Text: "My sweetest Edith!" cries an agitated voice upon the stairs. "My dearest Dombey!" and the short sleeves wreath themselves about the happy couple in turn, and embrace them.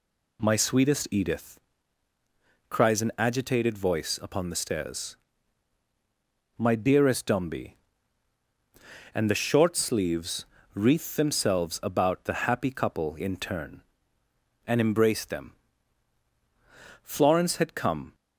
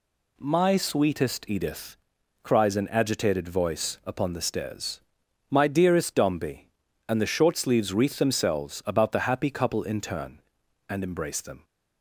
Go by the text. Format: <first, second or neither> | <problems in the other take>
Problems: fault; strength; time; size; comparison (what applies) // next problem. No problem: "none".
second | pauses between "sleeves" and "wreath"; slight; at 10.4 s; 0.26 s long // goes on to say "Florence had come"; noticeable; from 17.0 s on; 1.1 s long